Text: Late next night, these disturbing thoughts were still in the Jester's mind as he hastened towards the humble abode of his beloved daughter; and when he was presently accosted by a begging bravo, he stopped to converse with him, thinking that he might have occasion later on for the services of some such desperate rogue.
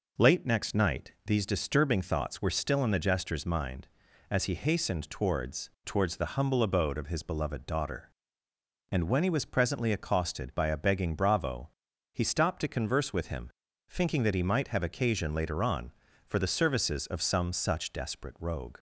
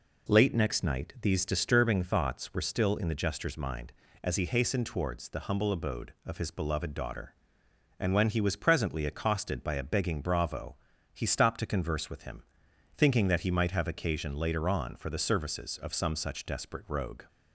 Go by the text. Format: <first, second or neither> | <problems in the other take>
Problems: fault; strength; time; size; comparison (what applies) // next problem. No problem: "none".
second | says "towards" twice; at 5.8 s